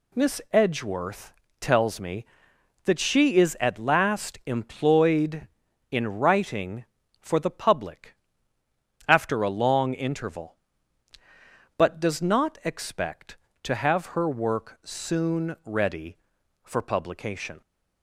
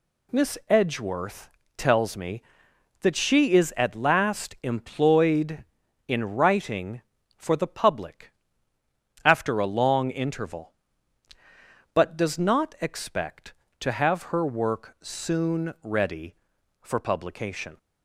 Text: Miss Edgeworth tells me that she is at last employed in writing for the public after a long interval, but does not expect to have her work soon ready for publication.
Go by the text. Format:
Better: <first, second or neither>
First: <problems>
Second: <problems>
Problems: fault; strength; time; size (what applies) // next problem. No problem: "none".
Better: neither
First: pauses between "Edgeworth" and "tells"; slight; at 1.3 s; 0.28 s long // pauses between "public" and "after"; noticeable; at 8.1 s; 0.94 s long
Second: pauses between "Edgeworth" and "tells"; slight; at 1.4 s; 0.28 s long // pauses between "public" and "after"; noticeable; at 8.3 s; 0.94 s long